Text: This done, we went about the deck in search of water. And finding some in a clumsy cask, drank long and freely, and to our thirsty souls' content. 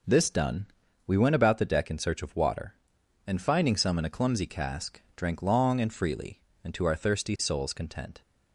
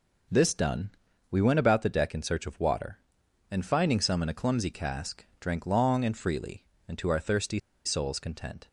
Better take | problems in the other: first | pauses between "thirsty" and "souls"; slight; at 7.5 s; 0.25 s long

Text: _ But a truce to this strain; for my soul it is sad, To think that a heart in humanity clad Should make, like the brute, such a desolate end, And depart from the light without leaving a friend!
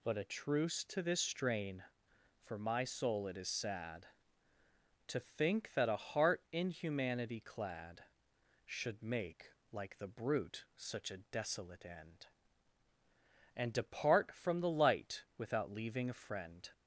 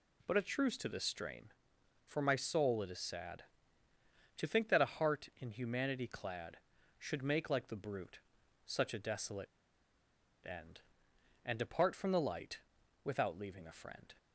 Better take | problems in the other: first | pauses between "desolate" and "end"; at 9.4 s; 0.98 s long // pauses between "light" and "without"; at 12.5 s; 0.44 s long

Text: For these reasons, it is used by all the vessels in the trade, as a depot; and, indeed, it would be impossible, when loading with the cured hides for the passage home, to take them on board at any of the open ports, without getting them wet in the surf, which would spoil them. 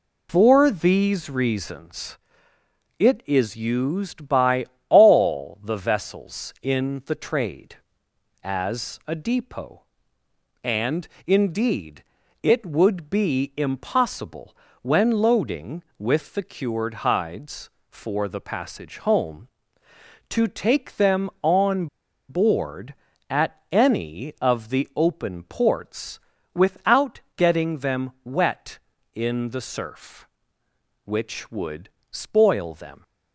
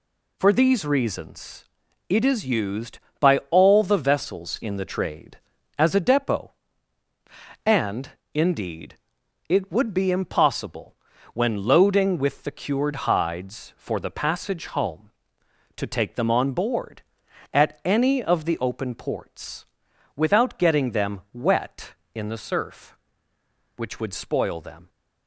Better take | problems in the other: second | pauses between "by" and "all"; slight; at 4.6 s; 0.22 s long // pauses between "on" and "board"; at 21.8 s; 0.42 s long // pauses between "at" and "any"; slight; at 23.5 s; 0.16 s long // pauses between "without" and "getting"; slight; at 27.1 s; 0.16 s long // pauses between "would" and "spoil"; slight; at 31.8 s; 0.24 s long

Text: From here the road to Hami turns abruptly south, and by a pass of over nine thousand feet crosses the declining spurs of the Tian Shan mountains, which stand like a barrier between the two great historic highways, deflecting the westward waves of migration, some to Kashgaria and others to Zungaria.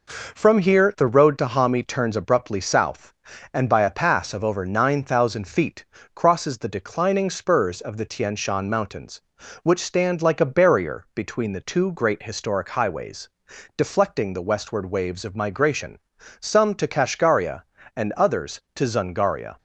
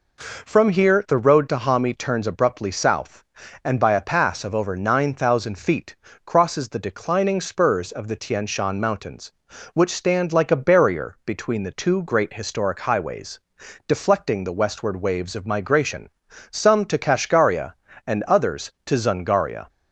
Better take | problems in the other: second | gets quieter; slight; throughout; 3 dB // pauses between "feet" and "crosses"; slight; at 5.8 s; 0.30 s long; slight in the second

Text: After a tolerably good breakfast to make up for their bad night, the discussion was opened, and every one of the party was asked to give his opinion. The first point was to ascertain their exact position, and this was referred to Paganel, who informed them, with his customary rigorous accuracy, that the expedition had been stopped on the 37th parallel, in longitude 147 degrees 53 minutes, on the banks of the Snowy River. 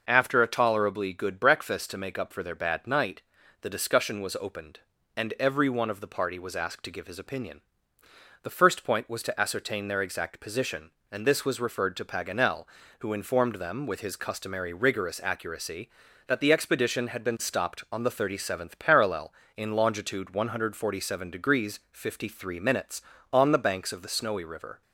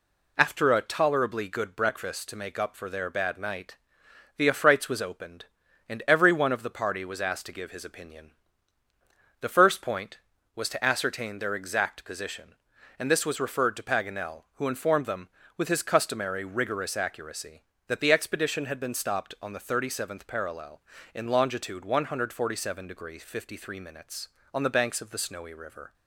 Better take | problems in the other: first | says "affrights" for "discussion"; at 4.4 s

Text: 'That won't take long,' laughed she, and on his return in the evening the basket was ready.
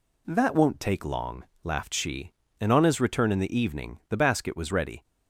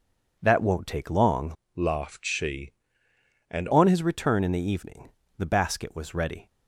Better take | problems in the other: first | changes voice from "laughed" to "and"; from 1.7 to 3.6 s; 1.9 s long // pauses between "evening" and "the"; slight; at 5.0 s; 0.28 s long

